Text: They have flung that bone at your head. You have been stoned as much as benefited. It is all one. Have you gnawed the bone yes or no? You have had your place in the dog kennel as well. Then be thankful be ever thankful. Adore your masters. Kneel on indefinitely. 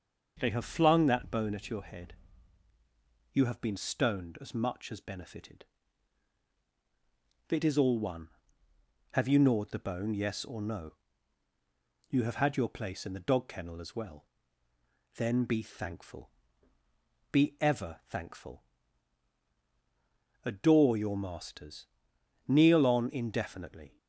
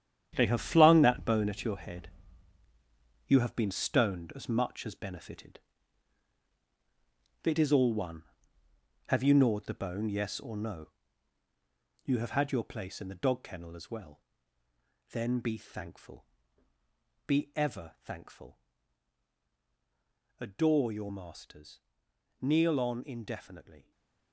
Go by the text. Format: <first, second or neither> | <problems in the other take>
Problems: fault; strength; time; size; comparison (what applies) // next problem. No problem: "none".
first | gets quieter; strong; throughout; 10 dB // starts louder than the rest; strong; until 1.3 s; 9.5 dB; noticeable in the first // pauses between "thankful" and "be"; at 16.2 s; 1.0 s long; also in the first // stays silent after the last word; slight; from 23.8 s on; 0.5 s long